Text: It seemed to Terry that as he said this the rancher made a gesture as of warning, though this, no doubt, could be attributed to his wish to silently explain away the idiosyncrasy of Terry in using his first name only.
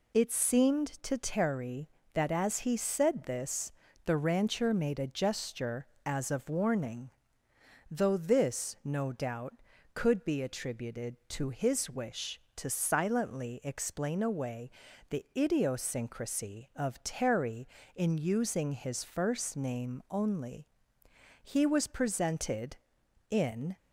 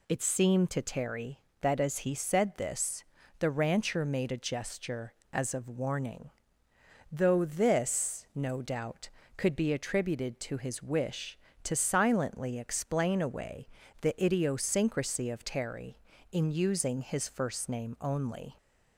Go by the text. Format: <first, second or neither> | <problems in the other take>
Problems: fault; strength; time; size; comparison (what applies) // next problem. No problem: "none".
second | pauses between "this" and "the"; slight; at 3.7 s; 0.36 s long; slight in the second // pauses between "away" and "the"; at 14.7 s; 0.40 s long; slight in the second // goes on to say "He was presented in"; strong; from 21.4 s on; 2.3 s long